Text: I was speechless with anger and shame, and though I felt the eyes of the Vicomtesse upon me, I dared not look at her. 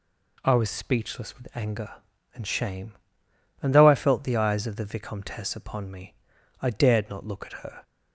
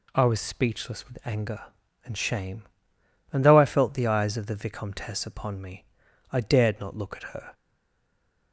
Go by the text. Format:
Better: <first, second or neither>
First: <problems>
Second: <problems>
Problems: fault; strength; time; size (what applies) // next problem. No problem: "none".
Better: first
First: none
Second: stays silent after the last word; from 7.5 s on; 1.0 s long